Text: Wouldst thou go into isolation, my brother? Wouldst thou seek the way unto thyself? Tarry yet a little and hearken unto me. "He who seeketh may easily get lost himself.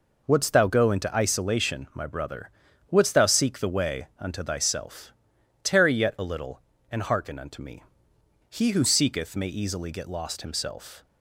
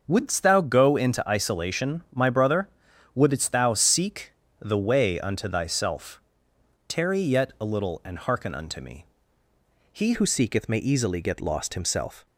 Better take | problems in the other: first | starts louder than the rest; noticeable; until 1.0 s; 6 dB // pauses between "seek" and "the"; slight; at 4.3 s; 0.28 s long // changes voice at "who"; from 10.1 s on; 2.1 s long

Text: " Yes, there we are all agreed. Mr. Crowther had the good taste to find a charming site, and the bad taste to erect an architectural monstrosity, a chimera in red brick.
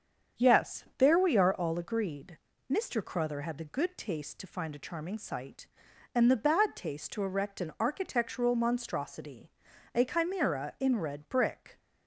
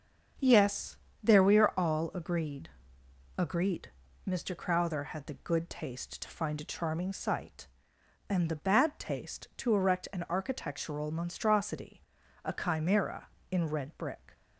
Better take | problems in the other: first | starts louder than the rest; strong; until 1.6 s; 7.5 dB; strong in the first // says "agreed" twice; at 3.3 s

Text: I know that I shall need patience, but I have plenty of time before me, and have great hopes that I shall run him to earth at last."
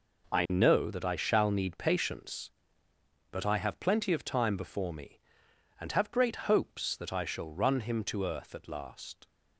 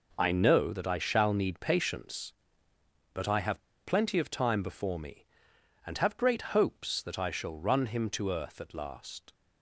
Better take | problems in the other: first | pauses between "have" and "plenty"; slight; at 3.6 s; 0.24 s long

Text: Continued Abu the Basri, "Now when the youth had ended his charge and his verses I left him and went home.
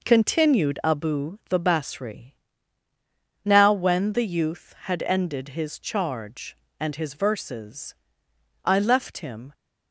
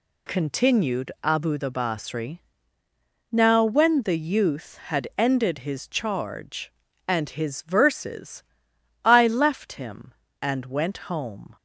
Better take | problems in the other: second | pauses between "verses" and "I"; noticeable; at 7.9 s; 0.69 s long; noticeable in the second // stops before "and went home"; at 9.5 s

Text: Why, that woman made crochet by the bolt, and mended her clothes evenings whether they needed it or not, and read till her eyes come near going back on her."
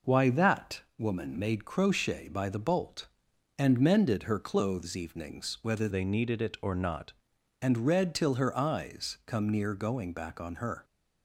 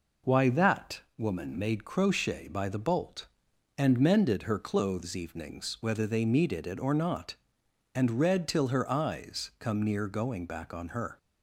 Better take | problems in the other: second | pauses between "that" and "woman"; slight; at 0.8 s; 0.18 s long; slight in the second // changes voice from "they" to "not"; from 5.9 to 7.1 s; 1.2 s long

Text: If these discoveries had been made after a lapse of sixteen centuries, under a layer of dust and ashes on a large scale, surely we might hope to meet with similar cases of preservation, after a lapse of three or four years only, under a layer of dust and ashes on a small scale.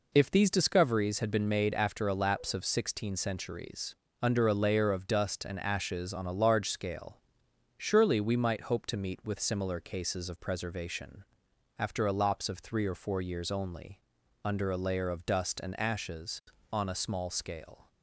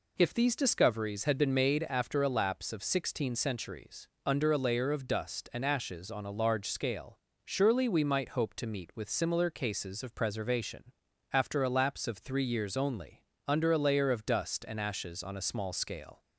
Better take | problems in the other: first | skips "or four"; at 12.4 s

